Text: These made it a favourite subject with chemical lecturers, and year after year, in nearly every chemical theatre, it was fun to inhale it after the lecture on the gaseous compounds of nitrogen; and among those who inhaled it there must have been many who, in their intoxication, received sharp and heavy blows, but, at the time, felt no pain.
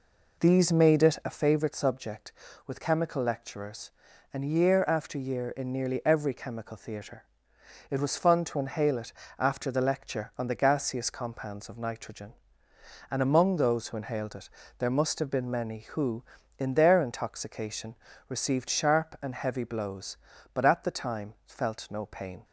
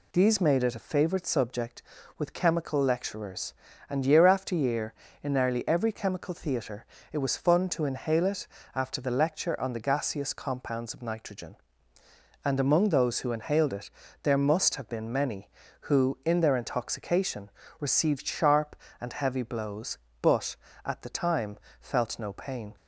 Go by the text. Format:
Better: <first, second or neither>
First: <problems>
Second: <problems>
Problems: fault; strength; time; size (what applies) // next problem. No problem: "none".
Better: second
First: starts louder than the rest; noticeable; until 1.4 s; 4 dB // pauses between "it" and "after"; slight; at 9.1 s; 0.26 s long // pauses between "it" and "there"; slight; at 14.5 s; 0.26 s long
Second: pauses between "it" and "after"; slight; at 8.4 s; 0.28 s long // pauses between "it" and "there"; slight; at 13.9 s; 0.32 s long